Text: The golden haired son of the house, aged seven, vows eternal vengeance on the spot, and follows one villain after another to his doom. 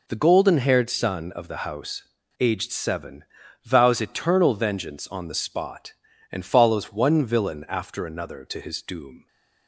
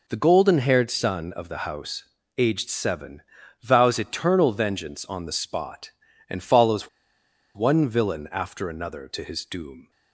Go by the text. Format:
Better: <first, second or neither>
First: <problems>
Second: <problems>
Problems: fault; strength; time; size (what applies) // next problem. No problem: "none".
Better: first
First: none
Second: pauses between "follows" and "one"; noticeable; at 6.8 s; 0.67 s long